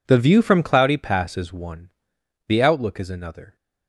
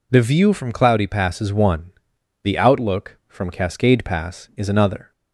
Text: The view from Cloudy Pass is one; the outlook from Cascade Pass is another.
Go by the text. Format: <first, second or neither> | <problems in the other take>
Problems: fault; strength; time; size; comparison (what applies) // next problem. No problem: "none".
second | skips "from Cascade Pass"; at 2.9 s